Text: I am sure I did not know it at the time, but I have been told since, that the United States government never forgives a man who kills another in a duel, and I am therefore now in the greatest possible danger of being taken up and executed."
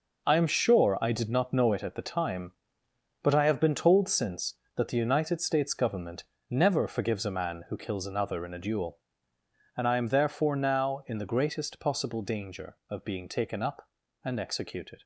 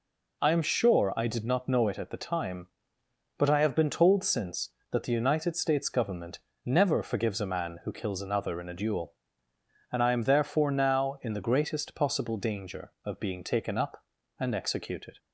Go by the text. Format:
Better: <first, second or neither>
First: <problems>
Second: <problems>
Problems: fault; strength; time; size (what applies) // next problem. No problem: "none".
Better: second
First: gets quieter; strong; throughout; 10 dB // pauses between "government" and "never"; slight; at 6.2 s; 0.26 s long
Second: pauses between "government" and "never"; slight; at 6.3 s; 0.26 s long